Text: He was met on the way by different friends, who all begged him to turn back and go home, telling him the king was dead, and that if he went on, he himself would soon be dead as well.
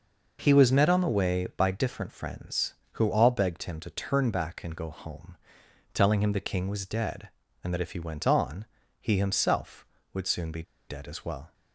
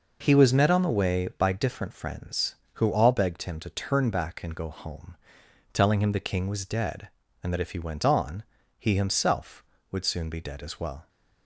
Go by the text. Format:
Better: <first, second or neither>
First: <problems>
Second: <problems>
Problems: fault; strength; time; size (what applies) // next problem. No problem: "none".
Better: second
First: pauses between "be" and "dead"; slight; at 10.6 s; 0.26 s long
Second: none